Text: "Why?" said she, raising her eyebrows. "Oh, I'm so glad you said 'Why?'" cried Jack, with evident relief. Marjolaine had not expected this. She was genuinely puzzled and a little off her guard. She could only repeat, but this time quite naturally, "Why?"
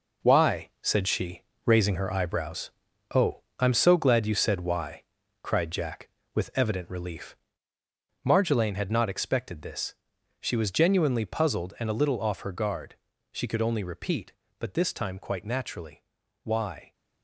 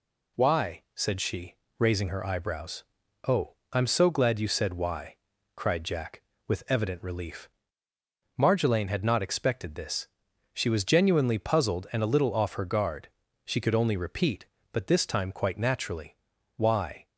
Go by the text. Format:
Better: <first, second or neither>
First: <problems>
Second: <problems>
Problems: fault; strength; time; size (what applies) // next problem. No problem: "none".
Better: second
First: gets quieter; strong; throughout; 8.5 dB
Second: none